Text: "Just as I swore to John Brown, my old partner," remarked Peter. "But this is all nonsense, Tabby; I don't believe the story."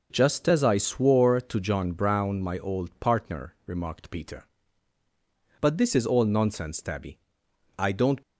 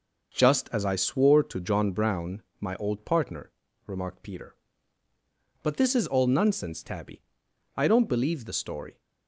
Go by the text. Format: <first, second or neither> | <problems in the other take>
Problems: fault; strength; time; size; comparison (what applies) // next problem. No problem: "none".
second | stops before "believe the story"; at 8.2 s